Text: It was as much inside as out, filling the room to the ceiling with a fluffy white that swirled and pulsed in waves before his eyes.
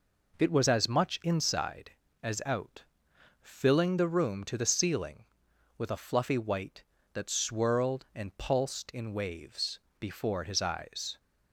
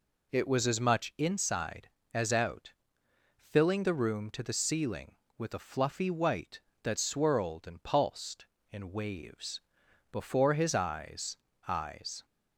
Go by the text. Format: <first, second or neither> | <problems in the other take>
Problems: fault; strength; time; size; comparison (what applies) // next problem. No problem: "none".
first | pauses between "waves" and "before"; noticeable; at 9.6 s; 0.50 s long; slight in the first // says "eyes" twice; at 11.6 s